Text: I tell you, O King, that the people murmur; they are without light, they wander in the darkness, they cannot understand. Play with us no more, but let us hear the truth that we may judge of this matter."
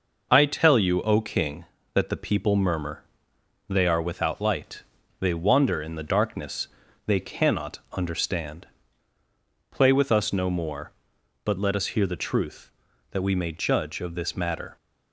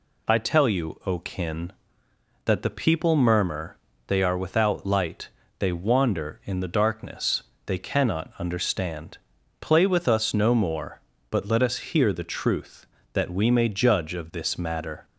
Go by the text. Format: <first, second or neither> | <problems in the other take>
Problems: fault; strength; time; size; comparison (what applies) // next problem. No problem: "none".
first | says "Kin" for "King"; at 1.1 s